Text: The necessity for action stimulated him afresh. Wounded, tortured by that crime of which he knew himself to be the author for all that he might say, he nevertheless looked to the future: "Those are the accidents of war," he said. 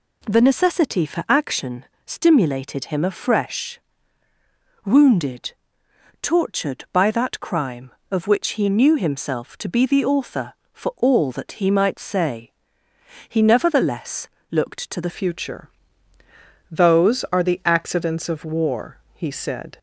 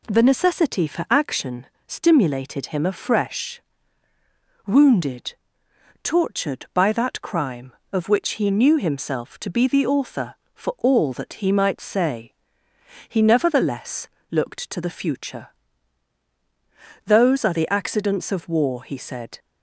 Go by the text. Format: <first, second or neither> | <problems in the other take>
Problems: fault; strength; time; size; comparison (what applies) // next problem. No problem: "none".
second | pauses between "action" and "stimulated"; slight; at 1.8 s; 0.22 s long; slight in the second // pauses between "nevertheless" and "looked"; slight; at 14.2 s; 0.20 s long; slight in the second // changes voice at "future"; from 15.0 s on; 4.7 s long